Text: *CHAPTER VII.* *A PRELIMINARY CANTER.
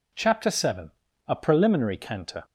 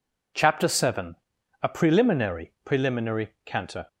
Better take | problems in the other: first | says "PRELIMINARY" twice; at 2.6 s

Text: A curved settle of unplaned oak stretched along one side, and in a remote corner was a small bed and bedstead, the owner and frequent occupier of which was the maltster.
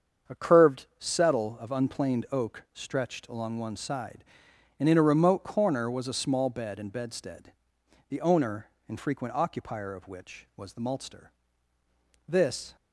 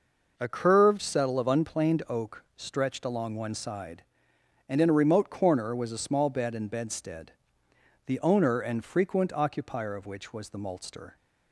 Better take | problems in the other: second | starts louder than the rest; strong; until 1.4 s; 7 dB // goes on to say "This"; slight; from 12.2 s on; 0.48 s long

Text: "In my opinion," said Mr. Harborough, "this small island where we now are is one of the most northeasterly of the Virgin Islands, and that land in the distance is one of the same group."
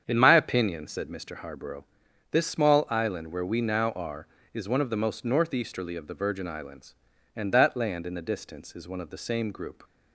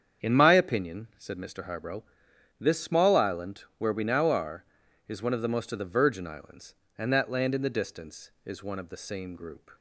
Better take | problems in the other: first | starts louder than the rest; strong; until 1.3 s; 8 dB; strong in the first // skips "northeasterly"; at 5.7 s

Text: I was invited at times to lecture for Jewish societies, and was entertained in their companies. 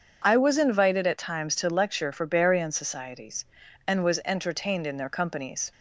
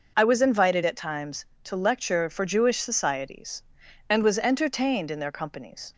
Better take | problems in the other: second | says "Barian" for "Jewish"; at 2.2 s

